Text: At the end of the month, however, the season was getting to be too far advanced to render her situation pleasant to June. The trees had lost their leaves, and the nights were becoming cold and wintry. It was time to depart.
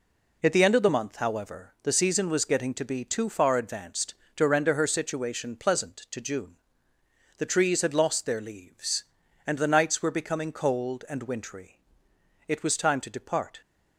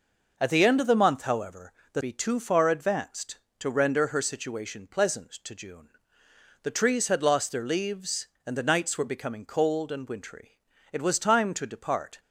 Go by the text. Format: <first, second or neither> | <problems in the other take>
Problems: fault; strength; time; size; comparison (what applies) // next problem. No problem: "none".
first | skips "season was getting to"; at 2.0 s